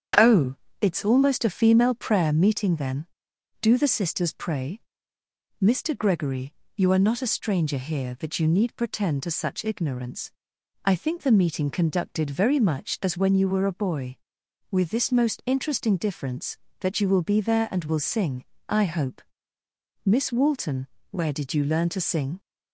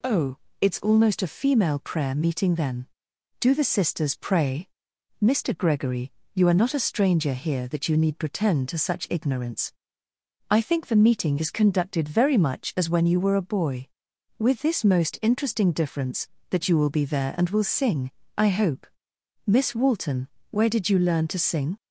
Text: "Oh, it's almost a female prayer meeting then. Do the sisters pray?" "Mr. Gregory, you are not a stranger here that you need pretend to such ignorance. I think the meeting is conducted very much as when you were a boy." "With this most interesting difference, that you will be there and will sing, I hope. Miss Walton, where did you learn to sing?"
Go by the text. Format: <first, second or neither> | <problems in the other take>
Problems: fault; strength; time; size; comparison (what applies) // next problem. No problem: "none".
second | starts louder than the rest; strong; until 1.4 s; 8.5 dB // skips "is"; at 11.7 s